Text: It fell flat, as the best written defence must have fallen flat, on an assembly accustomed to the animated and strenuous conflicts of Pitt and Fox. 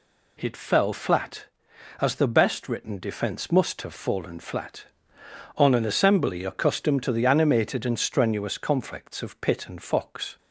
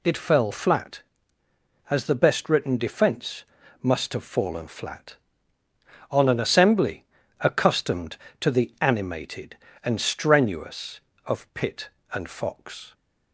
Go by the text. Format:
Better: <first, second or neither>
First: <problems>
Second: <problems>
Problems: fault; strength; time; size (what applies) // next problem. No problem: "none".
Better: first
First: none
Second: pauses between "defence" and "must"; at 3.4 s; 0.38 s long // pauses between "assembly" and "accustomed"; at 7.0 s; 0.38 s long // skips "conflicts"; at 11.1 s